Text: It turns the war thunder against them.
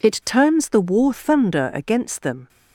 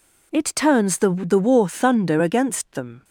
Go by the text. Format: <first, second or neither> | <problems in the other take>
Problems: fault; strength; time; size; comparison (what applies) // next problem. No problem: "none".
first | says "the" twice; at 1.1 s